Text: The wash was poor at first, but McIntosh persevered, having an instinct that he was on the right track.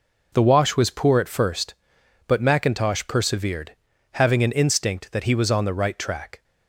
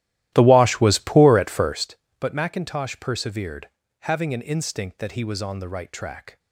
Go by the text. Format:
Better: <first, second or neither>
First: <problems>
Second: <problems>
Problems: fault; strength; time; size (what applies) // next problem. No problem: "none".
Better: first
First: none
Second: starts louder than the rest; strong; until 1.9 s; 14.5 dB